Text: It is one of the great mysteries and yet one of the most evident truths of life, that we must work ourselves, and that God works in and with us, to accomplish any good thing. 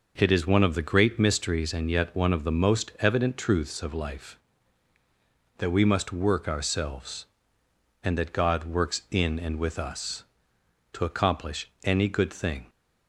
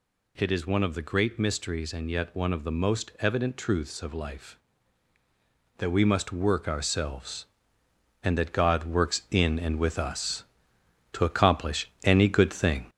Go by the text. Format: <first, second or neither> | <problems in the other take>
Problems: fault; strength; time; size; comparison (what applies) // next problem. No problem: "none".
first | gets louder; noticeable; throughout; 5 dB // pauses between "accomplish" and "any"; slight; at 11.8 s; 0.16 s long; slight in the first